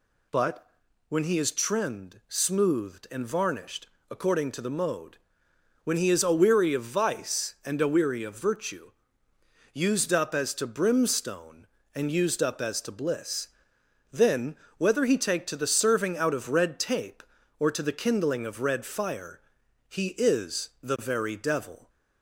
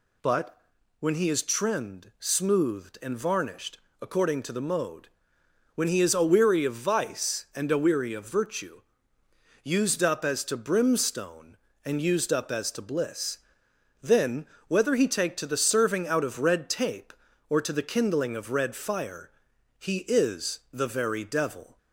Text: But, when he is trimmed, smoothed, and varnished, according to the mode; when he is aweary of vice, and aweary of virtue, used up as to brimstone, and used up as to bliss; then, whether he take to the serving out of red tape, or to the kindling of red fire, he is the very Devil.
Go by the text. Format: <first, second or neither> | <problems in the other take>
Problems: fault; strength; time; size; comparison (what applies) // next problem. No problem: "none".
neither | none